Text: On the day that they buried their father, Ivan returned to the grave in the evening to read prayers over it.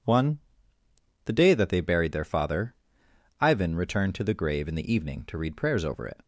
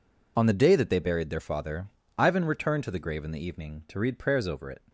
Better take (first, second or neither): second